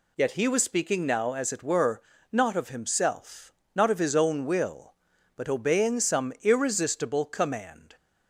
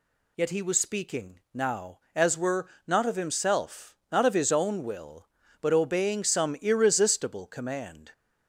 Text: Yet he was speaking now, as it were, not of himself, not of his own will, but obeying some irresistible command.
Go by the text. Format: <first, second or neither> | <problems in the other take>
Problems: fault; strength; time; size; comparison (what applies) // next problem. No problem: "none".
first | skips "it"; at 2.3 s